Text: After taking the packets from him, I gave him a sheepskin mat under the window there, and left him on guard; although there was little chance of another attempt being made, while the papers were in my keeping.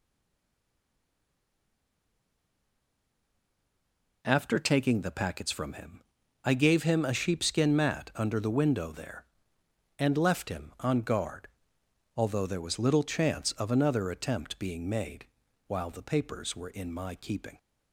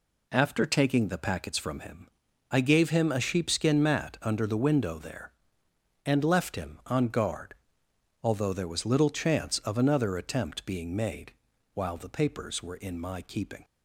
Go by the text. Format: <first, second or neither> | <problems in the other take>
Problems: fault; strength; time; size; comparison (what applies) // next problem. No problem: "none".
second | stays silent before the first word; strong; until 4.2 s; 4.2 s long